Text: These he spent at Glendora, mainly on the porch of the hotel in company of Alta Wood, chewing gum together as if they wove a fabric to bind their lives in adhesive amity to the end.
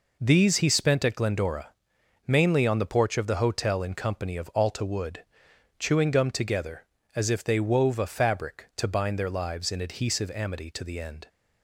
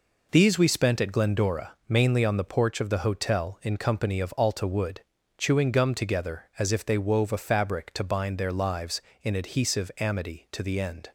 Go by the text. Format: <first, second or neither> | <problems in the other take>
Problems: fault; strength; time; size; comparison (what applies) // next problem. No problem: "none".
first | says "we" for "he"; at 0.5 s